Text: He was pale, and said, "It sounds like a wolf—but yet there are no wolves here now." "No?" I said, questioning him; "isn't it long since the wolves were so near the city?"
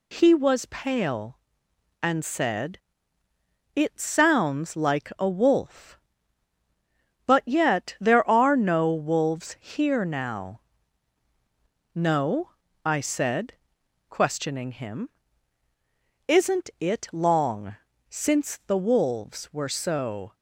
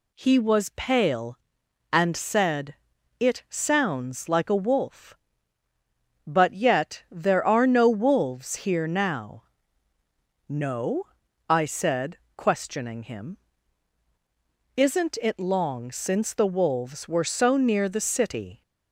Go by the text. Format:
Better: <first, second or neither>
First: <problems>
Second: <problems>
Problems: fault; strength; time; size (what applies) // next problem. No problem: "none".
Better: second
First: pauses between "long" and "since"; slight; at 17.7 s; 0.34 s long // stops before "near the city"; at 20.3 s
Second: none